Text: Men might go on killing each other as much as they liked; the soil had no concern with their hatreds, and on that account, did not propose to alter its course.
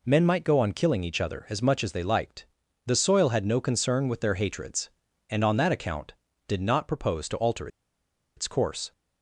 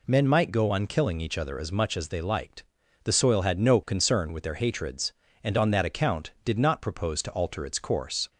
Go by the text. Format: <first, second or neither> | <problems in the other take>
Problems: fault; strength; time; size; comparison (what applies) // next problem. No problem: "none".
second | pauses between "alter" and "its"; noticeable; at 7.6 s; 0.69 s long